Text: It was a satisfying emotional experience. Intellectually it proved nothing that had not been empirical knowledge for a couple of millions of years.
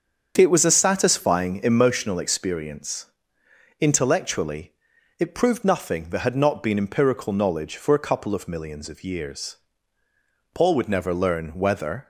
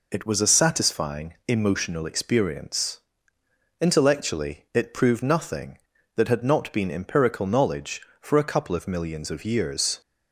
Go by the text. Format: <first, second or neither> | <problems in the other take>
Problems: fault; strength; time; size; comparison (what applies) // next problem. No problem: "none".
second | starts louder than the rest; strong; until 1.3 s; 7 dB // pauses between "Intellectually" and "it"; noticeable; at 4.7 s; 0.46 s long // goes on to say "Paul would never learn whether"; from 10.5 s on; 1.5 s long